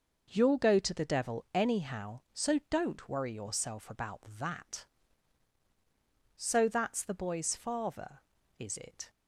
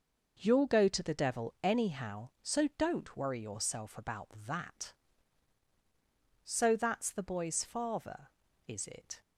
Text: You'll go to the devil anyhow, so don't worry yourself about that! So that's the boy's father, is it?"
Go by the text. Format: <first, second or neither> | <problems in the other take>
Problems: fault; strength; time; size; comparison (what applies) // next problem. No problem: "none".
neither | none